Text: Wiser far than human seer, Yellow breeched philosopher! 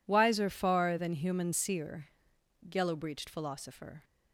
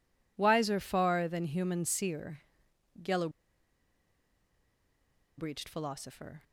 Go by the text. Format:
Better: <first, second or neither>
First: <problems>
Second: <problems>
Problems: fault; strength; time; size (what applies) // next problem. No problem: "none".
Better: first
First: none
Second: pauses between "Yellow" and "breeched"; strong; at 3.2 s; 2.0 s long